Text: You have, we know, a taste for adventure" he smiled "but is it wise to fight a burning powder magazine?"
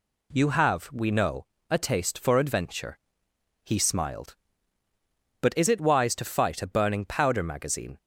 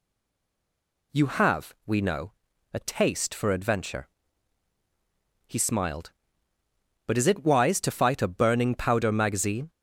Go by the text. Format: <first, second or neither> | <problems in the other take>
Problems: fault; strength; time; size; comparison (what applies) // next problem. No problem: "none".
first | stays silent before the first word; until 1.1 s; 1.1 s long // pauses between "adventure" and "he"; strong; at 4.0 s; 1.4 s long; noticeable in the first